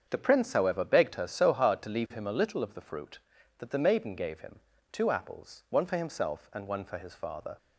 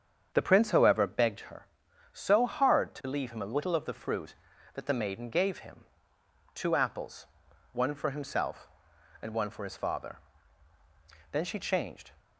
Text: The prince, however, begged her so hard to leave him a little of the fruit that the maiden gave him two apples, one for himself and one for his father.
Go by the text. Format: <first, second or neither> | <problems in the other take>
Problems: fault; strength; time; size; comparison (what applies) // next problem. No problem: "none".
first | starts louder than the rest; strong; until 1.3 s; 7.5 dB; strong in the first // pauses between "him" and "two"; noticeable; at 5.8 s; 0.74 s long; slight in the first // goes on to say "Then she changed"; noticeable; from 11.3 s on; 0.82 s long